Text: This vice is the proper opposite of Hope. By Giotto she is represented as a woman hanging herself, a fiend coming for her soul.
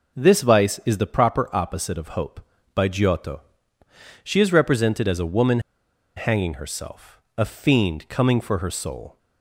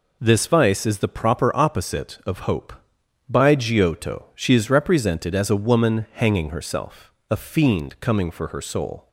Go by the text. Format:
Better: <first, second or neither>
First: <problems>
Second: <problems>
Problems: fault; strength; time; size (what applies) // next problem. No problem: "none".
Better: second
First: pauses between "Giotto" and "she"; noticeable; at 3.4 s; 0.82 s long // pauses between "woman" and "hanging"; noticeable; at 5.5 s; 0.57 s long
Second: none